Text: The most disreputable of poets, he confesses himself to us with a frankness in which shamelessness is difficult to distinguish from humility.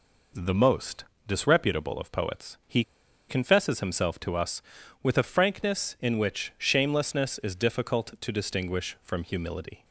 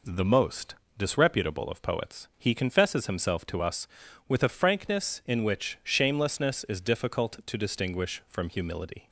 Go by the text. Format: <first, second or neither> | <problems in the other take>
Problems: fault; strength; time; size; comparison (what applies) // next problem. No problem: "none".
second | pauses between "most" and "disreputable"; slight; at 1.0 s; 0.24 s long; slight in the second // pauses between "he" and "confesses"; noticeable; at 2.8 s; 0.46 s long